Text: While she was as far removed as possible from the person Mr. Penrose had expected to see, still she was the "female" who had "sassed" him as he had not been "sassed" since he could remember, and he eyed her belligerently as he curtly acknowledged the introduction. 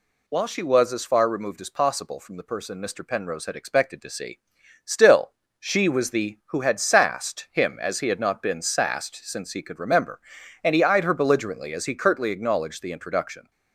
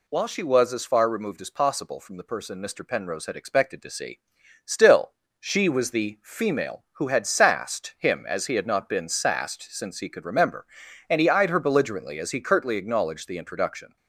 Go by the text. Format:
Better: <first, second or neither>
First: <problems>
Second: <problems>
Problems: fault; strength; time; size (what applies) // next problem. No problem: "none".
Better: second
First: pauses between "still" and "she"; slight; at 5.3 s; 0.30 s long // skips "female"; at 6.4 s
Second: pauses between "still" and "she"; slight; at 5.1 s; 0.30 s long